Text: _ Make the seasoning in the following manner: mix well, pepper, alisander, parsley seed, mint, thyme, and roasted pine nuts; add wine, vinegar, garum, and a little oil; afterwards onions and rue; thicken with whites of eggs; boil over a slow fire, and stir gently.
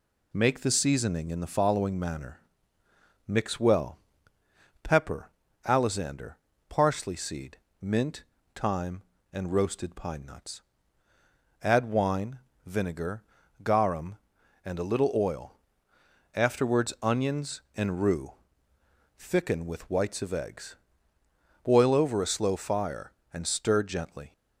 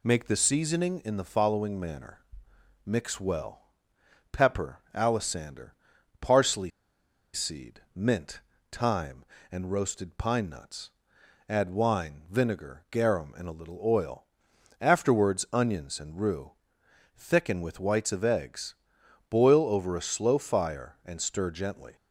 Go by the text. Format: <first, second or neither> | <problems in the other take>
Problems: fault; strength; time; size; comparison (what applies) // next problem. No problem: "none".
first | pauses between "parsley" and "seed"; noticeable; at 6.7 s; 0.63 s long